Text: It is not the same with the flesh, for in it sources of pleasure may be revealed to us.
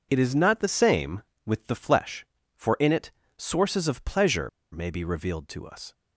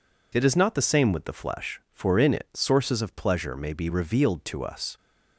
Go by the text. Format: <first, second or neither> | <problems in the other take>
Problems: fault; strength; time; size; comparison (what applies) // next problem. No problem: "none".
second | pauses between "it" and "sources"; slight; at 3.1 s; 0.26 s long // pauses between "pleasure" and "may"; slight; at 4.4 s; 0.23 s long